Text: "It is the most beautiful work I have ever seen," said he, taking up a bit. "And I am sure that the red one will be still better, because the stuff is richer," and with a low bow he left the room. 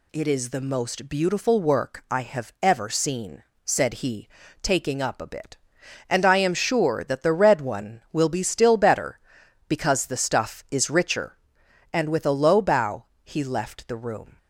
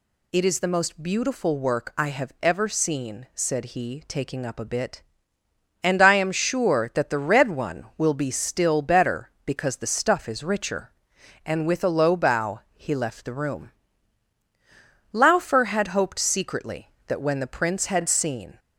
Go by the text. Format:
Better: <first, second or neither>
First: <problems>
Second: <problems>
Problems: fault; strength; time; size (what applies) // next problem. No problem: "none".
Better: first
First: pauses between "bow" and "he"; slight; at 13.0 s; 0.18 s long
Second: pauses between "bow" and "he"; slight; at 12.5 s; 0.16 s long // goes on to say "Laufer had hoped secretly that when the prince had seen"; strong; from 15.1 s on; 3.4 s long